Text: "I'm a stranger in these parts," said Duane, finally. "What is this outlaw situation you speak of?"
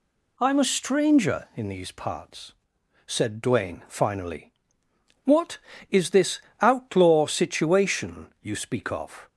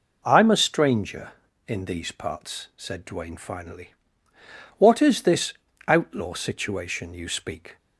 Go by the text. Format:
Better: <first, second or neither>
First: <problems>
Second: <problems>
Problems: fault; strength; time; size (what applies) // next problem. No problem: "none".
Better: first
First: pauses between "this" and "outlaw"; slight; at 6.4 s; 0.19 s long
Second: pauses between "this" and "outlaw"; slight; at 5.5 s; 0.34 s long // stops before "of"; at 7.7 s